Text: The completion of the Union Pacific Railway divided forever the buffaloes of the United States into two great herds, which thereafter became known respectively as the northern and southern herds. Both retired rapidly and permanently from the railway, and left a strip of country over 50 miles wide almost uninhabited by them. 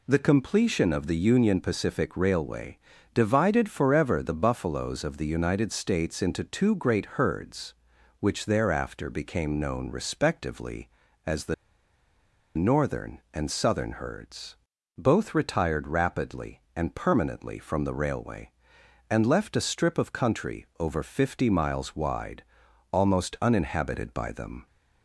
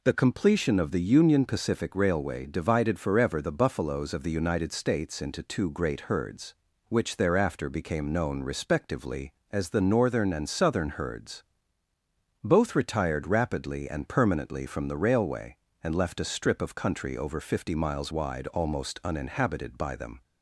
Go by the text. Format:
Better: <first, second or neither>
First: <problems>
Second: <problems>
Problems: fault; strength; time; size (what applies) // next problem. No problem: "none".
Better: second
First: pauses between "Railway" and "divided"; slight; at 2.7 s; 0.36 s long // pauses between "the" and "northern"; at 11.5 s; 1.0 s long // pauses between "wide" and "almost"; noticeable; at 22.4 s; 0.48 s long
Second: none